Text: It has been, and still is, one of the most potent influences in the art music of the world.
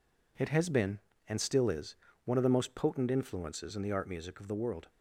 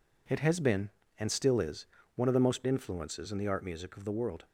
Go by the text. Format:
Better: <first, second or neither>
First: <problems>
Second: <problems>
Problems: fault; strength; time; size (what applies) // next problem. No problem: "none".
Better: first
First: none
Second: skips "potent"; at 2.6 s